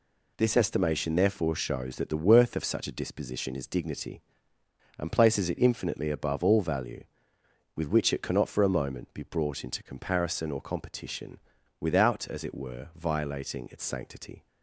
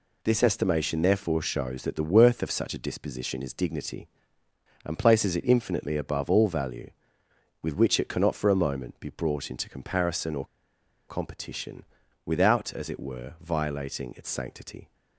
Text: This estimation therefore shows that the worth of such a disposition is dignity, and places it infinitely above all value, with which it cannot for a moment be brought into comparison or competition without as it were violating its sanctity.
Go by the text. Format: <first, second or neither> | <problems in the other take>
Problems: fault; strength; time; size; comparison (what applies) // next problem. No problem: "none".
first | pauses between "or" and "competition"; noticeable; at 10.4 s; 0.63 s long // pauses between "competition" and "without"; at 11.8 s; 0.40 s long; also in the first